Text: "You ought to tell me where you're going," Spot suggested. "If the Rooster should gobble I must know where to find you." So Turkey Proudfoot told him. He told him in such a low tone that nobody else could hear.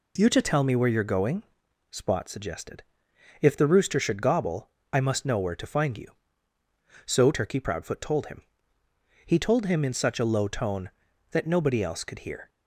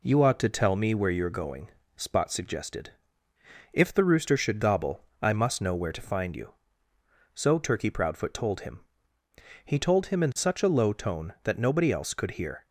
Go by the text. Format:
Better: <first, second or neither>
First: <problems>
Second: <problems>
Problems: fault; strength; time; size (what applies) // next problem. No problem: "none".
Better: second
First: skips "ought"; at 0.3 s // pauses between "gobble" and "I"; slight; at 4.7 s; 0.20 s long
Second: pauses between "gobble" and "I"; slight; at 5.0 s; 0.18 s long